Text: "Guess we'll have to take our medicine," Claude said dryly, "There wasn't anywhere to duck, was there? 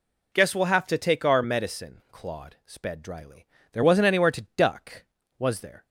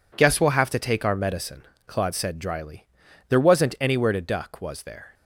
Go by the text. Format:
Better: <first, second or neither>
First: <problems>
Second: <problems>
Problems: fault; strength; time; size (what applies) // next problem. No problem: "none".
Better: second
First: says "sped" for "said"; at 2.6 s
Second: none